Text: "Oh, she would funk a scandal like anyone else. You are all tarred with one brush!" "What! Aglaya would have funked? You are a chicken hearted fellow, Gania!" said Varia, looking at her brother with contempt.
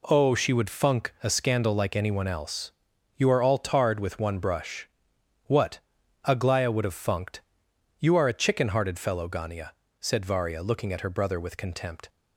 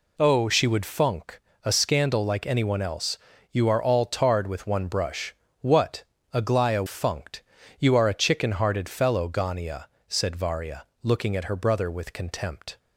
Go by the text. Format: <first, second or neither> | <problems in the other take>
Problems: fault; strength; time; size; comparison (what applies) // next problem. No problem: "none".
first | pauses between "funk" and "a"; slight; at 1.4 s; 0.24 s long // skips "would have"; at 6.8 s